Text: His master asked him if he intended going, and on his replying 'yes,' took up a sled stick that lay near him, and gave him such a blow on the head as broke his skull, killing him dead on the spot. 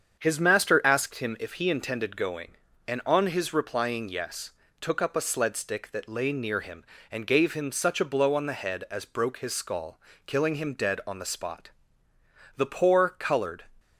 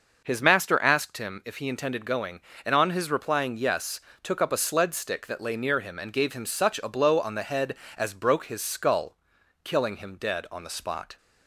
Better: second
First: starts louder than the rest; strong; until 1.2 s; 7.5 dB // goes on to say "The poor colored"; noticeable; from 12.5 s on; 1.1 s long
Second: none

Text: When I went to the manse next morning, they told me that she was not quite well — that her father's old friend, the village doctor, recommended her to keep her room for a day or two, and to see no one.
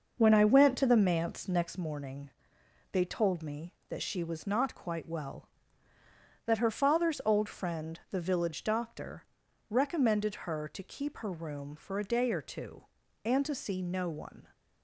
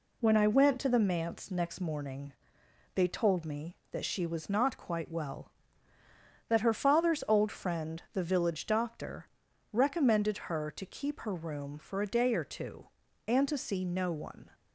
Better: second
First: starts louder than the rest; noticeable; until 1.7 s; 6 dB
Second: none

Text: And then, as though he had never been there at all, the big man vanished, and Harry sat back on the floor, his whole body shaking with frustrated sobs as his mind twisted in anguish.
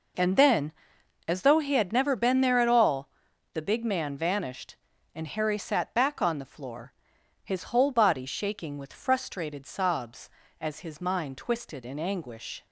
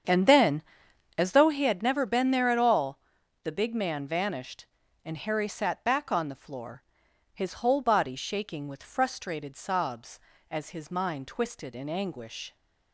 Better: first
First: none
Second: starts louder than the rest; strong; until 1.7 s; 7.5 dB

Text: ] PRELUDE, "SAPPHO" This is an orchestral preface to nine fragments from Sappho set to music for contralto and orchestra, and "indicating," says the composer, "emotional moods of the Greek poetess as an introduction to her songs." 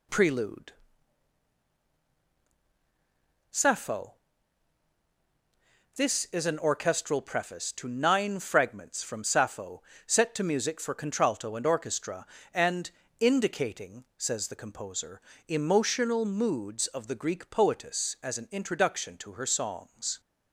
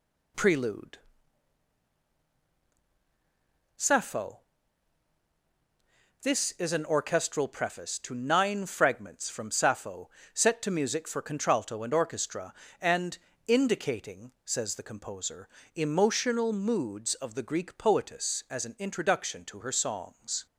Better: neither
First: pauses between "SAPPHO" and "This"; strong; at 4.1 s; 1.8 s long // pauses between "Sappho" and "set"; slight; at 9.8 s; 0.24 s long // pauses between "and" and "indicating"; slight; at 12.9 s; 0.30 s long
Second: pauses between "SAPPHO" and "This"; strong; at 4.3 s; 1.8 s long // pauses between "Sappho" and "set"; slight; at 10.0 s; 0.24 s long // pauses between "and" and "indicating"; slight; at 13.1 s; 0.30 s long

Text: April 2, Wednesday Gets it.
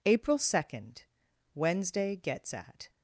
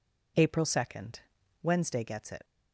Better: second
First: says "at" for "it"; at 2.5 s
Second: none

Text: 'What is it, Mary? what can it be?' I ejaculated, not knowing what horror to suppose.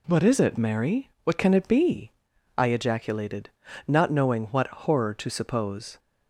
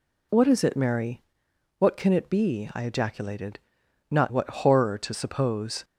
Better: first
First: none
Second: skips "knowing"; at 4.3 s

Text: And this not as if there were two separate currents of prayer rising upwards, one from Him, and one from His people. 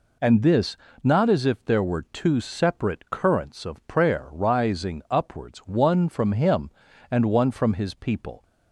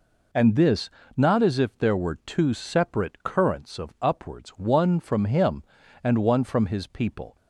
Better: first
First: pauses between "this" and "not"; slight; at 0.7 s; 0.28 s long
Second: pauses between "this" and "not"; slight; at 0.8 s; 0.28 s long // skips "prayer rising"; at 3.9 s

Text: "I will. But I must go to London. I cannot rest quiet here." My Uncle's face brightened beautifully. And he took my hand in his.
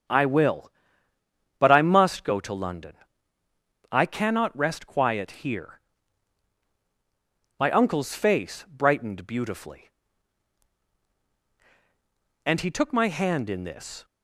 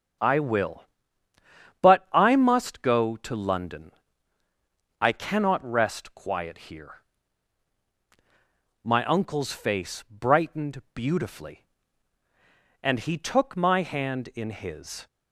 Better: second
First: starts louder than the rest; strong; until 1.9 s; 7.5 dB // says "this" for "his"; at 13.6 s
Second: starts louder than the rest; strong; until 2.2 s; 7 dB

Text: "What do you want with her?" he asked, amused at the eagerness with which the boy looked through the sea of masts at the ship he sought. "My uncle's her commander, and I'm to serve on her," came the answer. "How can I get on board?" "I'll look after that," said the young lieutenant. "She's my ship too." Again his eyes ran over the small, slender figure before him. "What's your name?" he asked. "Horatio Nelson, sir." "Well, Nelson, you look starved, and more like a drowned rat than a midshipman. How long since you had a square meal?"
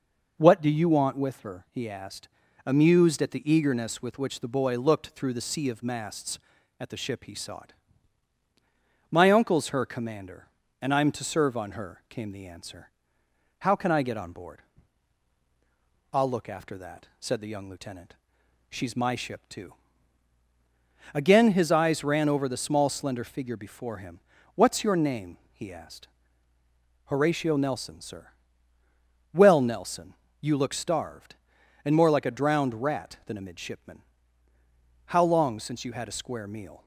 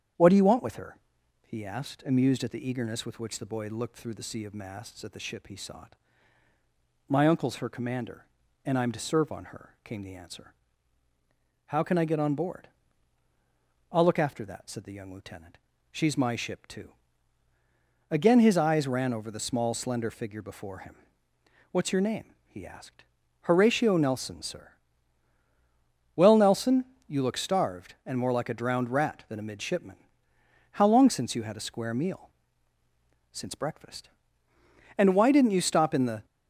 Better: first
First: none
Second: starts louder than the rest; strong; until 1.6 s; 8.5 dB // goes on to say "Since breakfast And why didn't you stop in the"; strong; from 33.3 s on; 2.9 s long

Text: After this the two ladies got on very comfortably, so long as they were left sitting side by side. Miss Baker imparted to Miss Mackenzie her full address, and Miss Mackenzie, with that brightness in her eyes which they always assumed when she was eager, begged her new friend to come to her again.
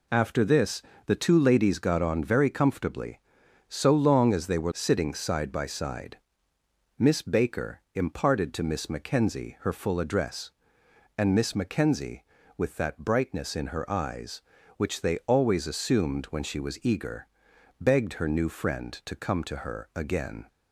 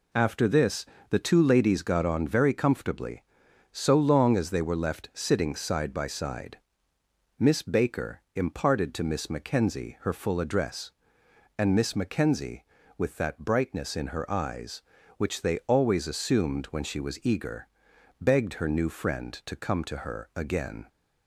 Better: second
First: pauses between "this" and "the"; slight; at 0.8 s; 0.26 s long // skips "left"; at 4.7 s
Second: pauses between "this" and "the"; slight; at 0.8 s; 0.26 s long

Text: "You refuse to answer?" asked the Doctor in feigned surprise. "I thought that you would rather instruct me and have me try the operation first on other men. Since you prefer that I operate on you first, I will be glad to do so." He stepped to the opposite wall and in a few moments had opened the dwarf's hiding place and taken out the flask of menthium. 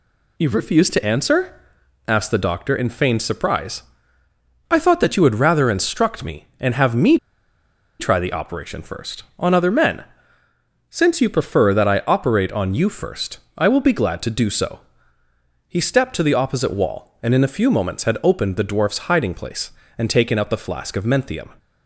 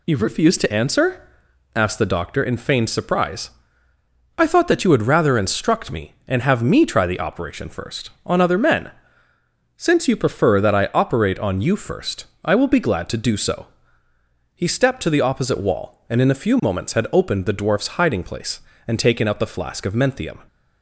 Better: second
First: pauses between "me" and "try"; noticeable; at 7.1 s; 0.83 s long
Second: none

